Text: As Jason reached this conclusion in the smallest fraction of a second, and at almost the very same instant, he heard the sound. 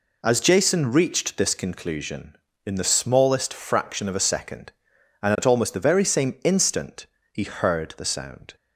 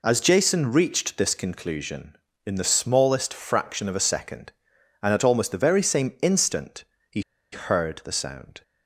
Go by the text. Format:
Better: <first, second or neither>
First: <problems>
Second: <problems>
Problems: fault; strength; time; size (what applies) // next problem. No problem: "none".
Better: first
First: none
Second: pauses between "he" and "heard"; slight; at 7.2 s; 0.31 s long